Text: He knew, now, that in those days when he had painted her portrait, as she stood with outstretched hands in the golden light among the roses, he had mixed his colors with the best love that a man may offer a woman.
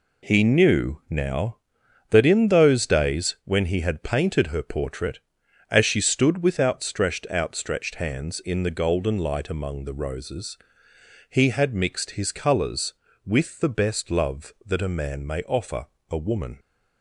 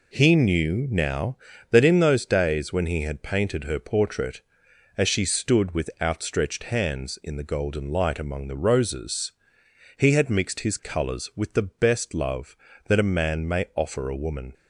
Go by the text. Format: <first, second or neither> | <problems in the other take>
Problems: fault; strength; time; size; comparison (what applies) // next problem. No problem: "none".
second | says "outstretched" twice; at 7.2 s // pauses between "offer" and "a"; slight; at 15.8 s; 0.22 s long